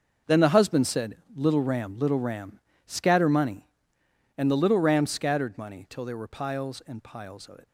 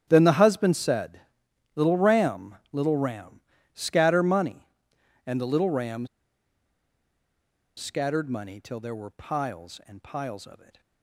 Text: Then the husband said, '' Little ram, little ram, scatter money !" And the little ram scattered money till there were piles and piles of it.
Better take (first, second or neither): first